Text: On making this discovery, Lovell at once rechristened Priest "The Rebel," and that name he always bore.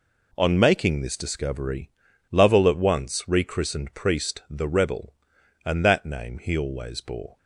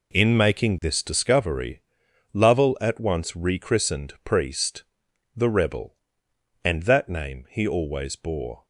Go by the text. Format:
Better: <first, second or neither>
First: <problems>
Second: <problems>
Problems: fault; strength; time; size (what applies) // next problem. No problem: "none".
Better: first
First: none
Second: says "In" for "On"; at 0.1 s // pauses between "Priest" and "The"; noticeable; at 4.8 s; 0.50 s long